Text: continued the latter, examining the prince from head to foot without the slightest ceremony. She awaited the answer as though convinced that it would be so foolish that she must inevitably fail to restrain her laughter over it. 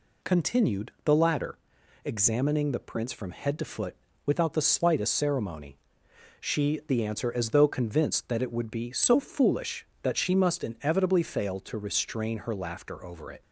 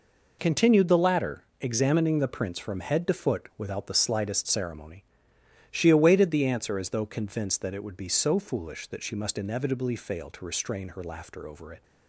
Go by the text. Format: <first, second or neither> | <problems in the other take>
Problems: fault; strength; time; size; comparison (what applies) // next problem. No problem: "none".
second | pauses between "foot" and "without"; slight; at 3.9 s; 0.30 s long // skips "awaited"; at 6.8 s